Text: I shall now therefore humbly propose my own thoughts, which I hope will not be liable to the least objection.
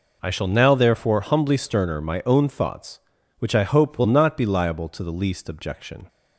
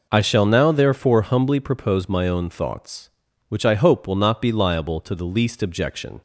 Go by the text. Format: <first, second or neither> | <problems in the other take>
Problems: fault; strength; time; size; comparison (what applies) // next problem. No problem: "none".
second | says "sterner" for "propose"; at 1.5 s